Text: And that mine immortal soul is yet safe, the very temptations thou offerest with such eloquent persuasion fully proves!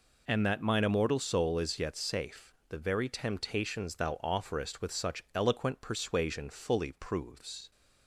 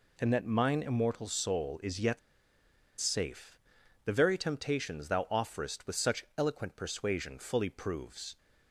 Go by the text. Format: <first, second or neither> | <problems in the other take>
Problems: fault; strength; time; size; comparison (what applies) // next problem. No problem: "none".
first | pauses between "yet" and "safe"; noticeable; at 2.1 s; 0.81 s long